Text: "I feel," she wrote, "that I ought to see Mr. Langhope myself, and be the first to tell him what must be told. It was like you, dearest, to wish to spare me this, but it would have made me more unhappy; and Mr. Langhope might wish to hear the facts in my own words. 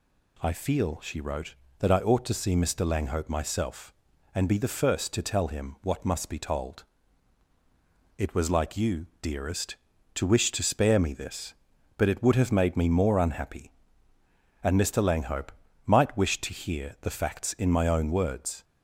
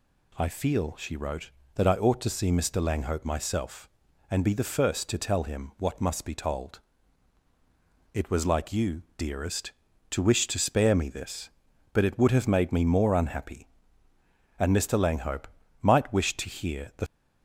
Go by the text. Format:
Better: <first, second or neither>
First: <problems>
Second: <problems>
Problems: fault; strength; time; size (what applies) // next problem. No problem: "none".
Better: first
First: pauses between "Langhope" and "might"; slight; at 15.5 s; 0.36 s long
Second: pauses between "Langhope" and "might"; slight; at 15.4 s; 0.36 s long // stops before "facts in my own words"; at 17.0 s